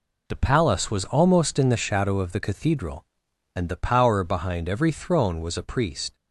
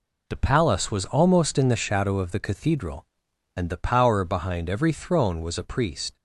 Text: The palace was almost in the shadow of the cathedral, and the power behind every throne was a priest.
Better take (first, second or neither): neither